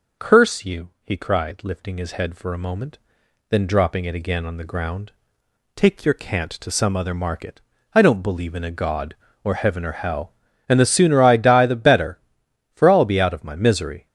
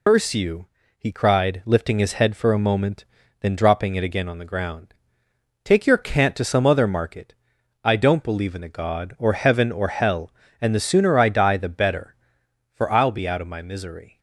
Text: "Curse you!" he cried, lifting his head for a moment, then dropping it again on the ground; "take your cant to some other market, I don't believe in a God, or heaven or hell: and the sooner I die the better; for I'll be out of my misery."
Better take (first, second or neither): first